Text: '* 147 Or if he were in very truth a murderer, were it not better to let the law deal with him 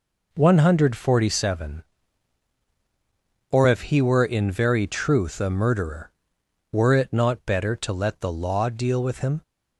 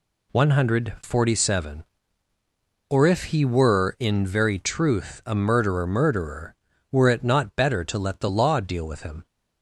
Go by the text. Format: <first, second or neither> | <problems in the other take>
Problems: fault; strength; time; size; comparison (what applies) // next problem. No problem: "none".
first | says "murderer" twice; at 5.8 s